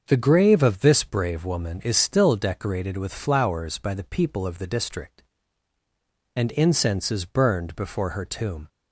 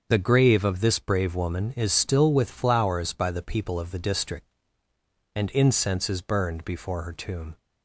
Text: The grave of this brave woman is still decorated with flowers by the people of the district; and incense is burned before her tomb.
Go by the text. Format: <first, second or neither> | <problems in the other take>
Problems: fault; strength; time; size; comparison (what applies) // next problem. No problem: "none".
first | starts louder than the rest; until 1.1 s; 7 dB; also in the first // skips "decorated"; at 2.3 s